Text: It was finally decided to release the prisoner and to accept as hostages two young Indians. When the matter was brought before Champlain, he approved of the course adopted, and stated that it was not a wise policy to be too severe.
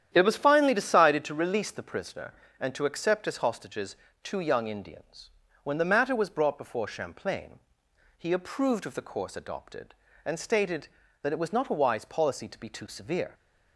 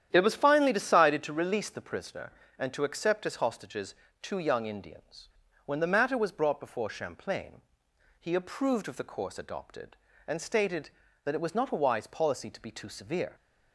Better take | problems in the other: neither | starts louder than the rest; strong; the same in both // pauses between "hostages" and "two"; slight; the same in both

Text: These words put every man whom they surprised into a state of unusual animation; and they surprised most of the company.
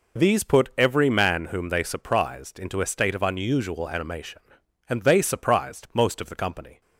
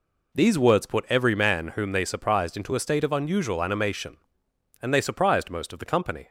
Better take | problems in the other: second | skips "words"; at 0.4 s

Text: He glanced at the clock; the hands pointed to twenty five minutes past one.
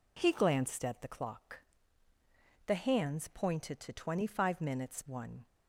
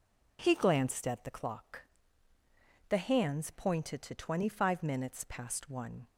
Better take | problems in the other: second | skips "past"; at 5.0 s

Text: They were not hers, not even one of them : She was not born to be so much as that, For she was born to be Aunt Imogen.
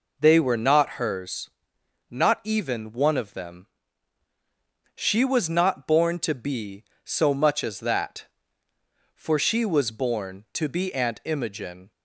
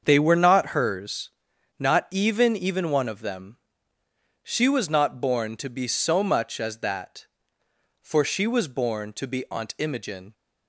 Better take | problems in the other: first | starts louder than the rest; until 1.0 s; 7 dB // says "even" twice; at 2.5 s

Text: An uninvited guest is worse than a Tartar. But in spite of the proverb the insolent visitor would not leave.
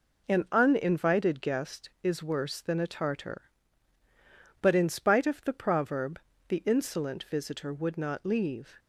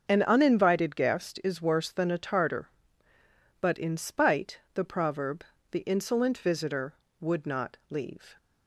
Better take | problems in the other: first | starts louder than the rest; until 1.1 s; 6.5 dB // skips "of"; at 4.6 s // pauses between "proverb" and "the"; slight; at 5.4 s; 0.26 s long; slight in the first

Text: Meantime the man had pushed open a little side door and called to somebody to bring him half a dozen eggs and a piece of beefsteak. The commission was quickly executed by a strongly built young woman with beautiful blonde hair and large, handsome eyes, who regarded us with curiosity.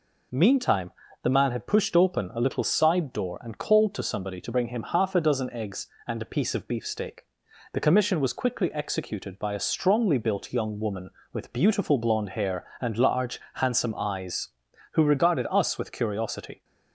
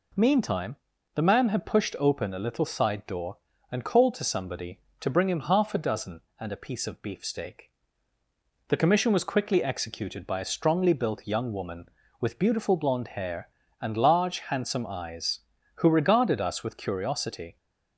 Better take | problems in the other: first | pauses between "Meantime" and "the"; at 0.7 s; 0.40 s long; slight in the first // skips "eggs"; at 6.2 s

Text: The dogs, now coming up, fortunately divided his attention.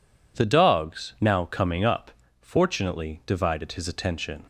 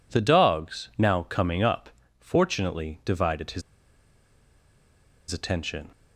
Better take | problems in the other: first | pauses between "his" and "attention"; strong; at 3.6 s; 1.6 s long

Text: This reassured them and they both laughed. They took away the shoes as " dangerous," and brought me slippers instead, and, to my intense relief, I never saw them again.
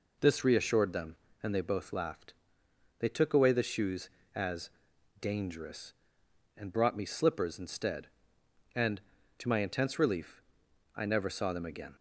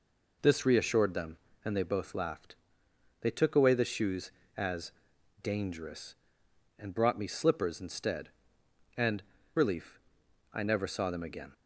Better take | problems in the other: first | skips "to my intense"; at 9.3 s

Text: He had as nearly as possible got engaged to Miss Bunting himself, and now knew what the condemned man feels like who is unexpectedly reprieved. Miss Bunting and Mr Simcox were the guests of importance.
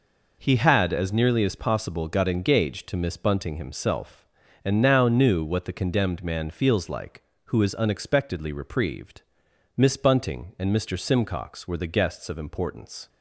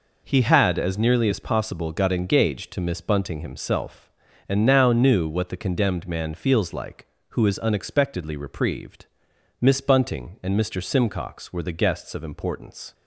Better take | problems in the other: neither | none

